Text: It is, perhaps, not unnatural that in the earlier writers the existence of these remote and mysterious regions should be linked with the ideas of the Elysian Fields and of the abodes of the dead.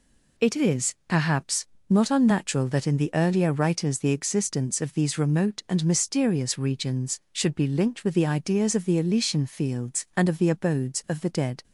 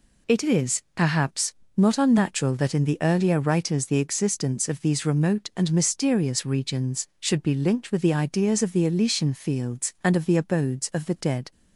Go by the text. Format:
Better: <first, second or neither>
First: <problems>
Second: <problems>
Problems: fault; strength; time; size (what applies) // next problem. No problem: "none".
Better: neither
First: none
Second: none